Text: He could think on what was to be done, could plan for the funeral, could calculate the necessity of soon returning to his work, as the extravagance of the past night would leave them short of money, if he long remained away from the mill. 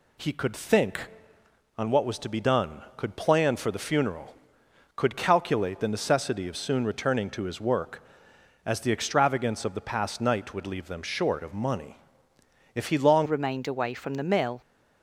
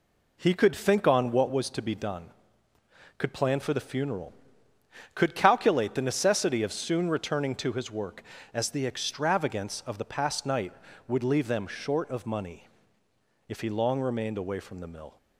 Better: second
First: changes voice at "remained"; from 13.2 s on; 1.4 s long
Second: none

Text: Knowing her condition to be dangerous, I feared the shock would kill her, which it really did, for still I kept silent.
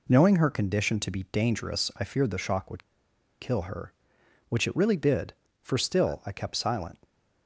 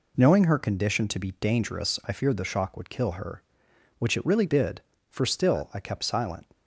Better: second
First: pauses between "would" and "kill"; noticeable; at 2.8 s; 0.59 s long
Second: none

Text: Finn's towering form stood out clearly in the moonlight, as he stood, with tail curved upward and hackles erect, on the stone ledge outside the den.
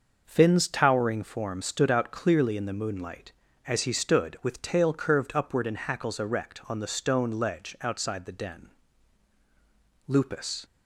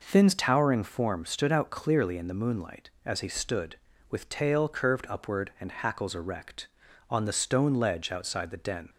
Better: second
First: goes on to say "Lupus"; from 10.0 s on; 0.58 s long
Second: none

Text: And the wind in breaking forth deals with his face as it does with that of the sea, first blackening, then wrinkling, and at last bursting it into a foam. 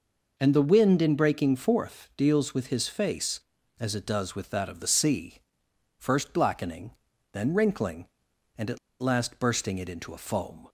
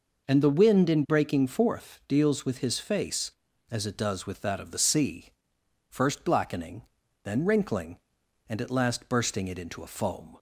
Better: second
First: pauses between "at" and "last"; slight; at 8.7 s; 0.22 s long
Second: none

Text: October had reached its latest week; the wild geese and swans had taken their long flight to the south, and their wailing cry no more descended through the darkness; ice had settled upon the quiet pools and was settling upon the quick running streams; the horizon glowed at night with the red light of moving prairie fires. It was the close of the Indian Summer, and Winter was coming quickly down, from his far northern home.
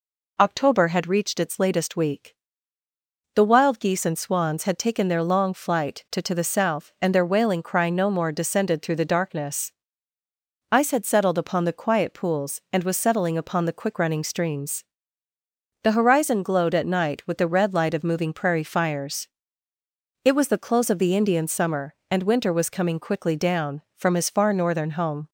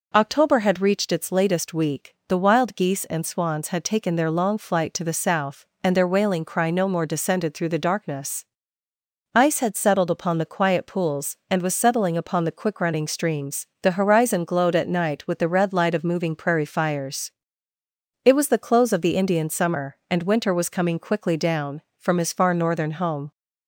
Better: second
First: says "to" twice; at 6.2 s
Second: none

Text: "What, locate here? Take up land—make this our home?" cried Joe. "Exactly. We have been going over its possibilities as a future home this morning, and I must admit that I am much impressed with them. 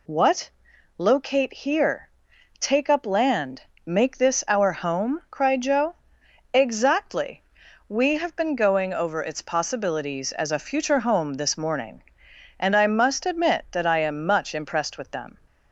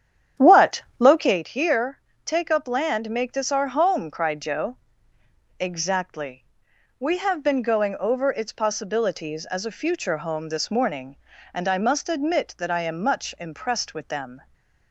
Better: first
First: none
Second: starts louder than the rest; strong; until 1.4 s; 9 dB // stays silent after the last word; slight; from 14.3 s on; 0.6 s long

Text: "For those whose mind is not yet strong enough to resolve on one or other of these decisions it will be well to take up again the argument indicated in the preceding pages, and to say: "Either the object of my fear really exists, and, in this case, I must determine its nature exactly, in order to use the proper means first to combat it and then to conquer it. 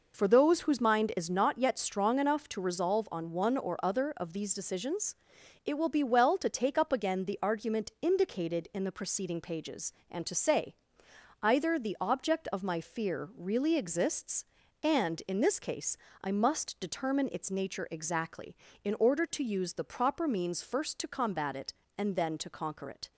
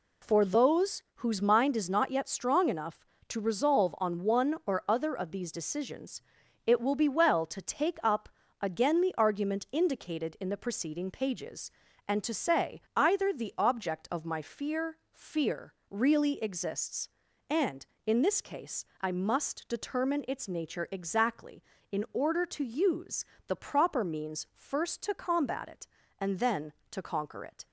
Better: first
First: pauses between "decisions" and "it"; noticeable; at 5.1 s; 0.52 s long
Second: pauses between "decisions" and "it"; at 6.2 s; 0.44 s long // pauses between "up" and "again"; slight; at 8.2 s; 0.32 s long // says "fear" twice; at 15.1 s // pauses between "use" and "the"; slight; at 23.2 s; 0.22 s long

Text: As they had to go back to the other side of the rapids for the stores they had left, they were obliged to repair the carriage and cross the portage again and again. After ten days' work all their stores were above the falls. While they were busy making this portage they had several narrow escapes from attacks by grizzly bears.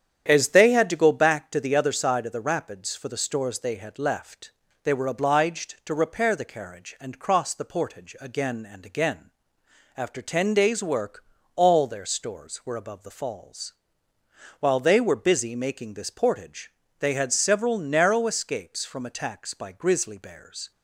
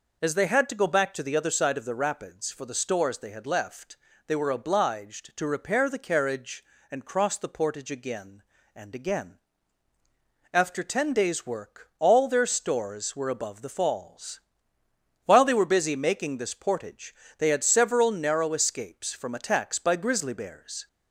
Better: second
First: starts louder than the rest; strong; until 1.4 s; 9 dB // pauses between "work" and "all"; slight; at 11.2 s; 0.32 s long // pauses between "portage" and "they"; slight; at 16.7 s; 0.26 s long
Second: pauses between "portage" and "they"; slight; at 17.1 s; 0.24 s long

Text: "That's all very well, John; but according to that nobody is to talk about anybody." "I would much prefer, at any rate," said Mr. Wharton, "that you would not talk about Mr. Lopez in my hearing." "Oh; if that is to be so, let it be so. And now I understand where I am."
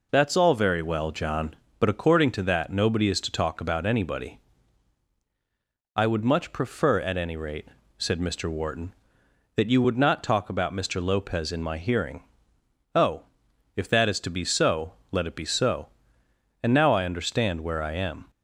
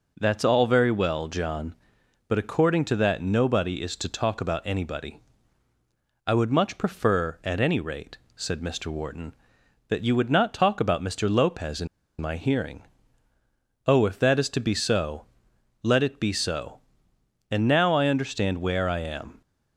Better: first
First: none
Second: pauses between "in" and "my"; slight; at 11.8 s; 0.33 s long

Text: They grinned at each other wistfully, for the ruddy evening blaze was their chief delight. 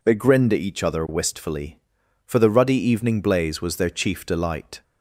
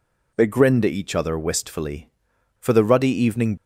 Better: first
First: none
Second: stops before "blaze was their chief delight"; at 3.5 s

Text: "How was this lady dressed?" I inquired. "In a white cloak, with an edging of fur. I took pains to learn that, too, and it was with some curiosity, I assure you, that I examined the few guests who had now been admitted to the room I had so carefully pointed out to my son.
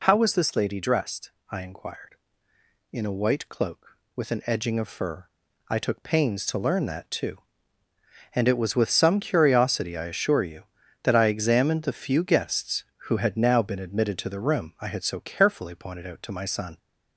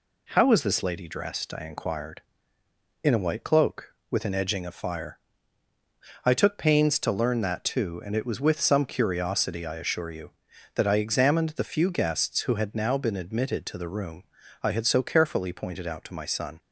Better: first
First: none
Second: says "fire" for "fur"; at 4.7 s // pauses between "room" and "I"; at 14.2 s; 0.40 s long

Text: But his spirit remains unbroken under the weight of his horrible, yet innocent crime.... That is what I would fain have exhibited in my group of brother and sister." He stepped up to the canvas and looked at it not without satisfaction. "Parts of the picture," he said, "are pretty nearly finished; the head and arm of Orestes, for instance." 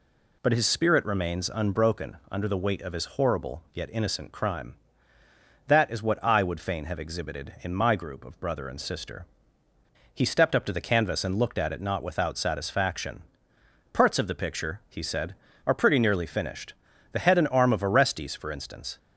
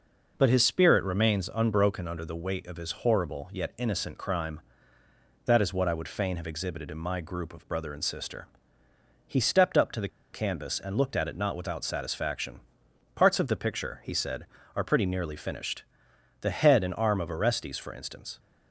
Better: first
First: none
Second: pauses between "the" and "canvas"; slight; at 10.0 s; 0.24 s long

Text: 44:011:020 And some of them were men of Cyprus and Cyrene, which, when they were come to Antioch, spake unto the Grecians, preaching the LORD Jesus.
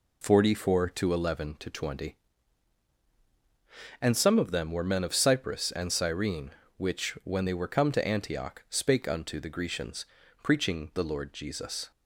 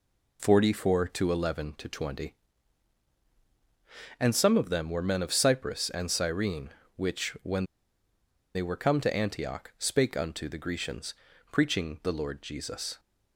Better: first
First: none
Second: pauses between "when" and "they"; noticeable; at 7.6 s; 0.90 s long

